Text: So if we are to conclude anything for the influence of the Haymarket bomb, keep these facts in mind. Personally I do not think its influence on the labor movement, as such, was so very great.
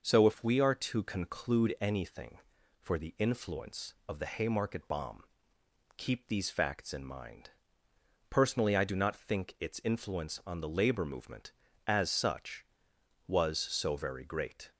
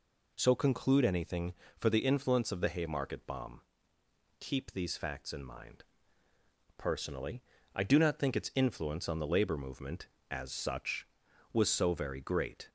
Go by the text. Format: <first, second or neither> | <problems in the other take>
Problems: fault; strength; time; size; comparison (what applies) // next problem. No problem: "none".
first | skips "if we are to"; at 0.5 s // pauses between "Personally" and "I"; slight; at 7.4 s; 0.34 s long